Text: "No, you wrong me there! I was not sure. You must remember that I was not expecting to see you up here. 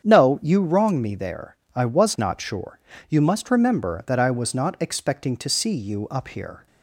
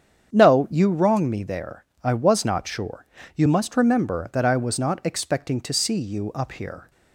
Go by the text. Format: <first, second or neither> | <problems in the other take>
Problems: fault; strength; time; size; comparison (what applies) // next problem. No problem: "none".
neither | starts louder than the rest; strong; the same in both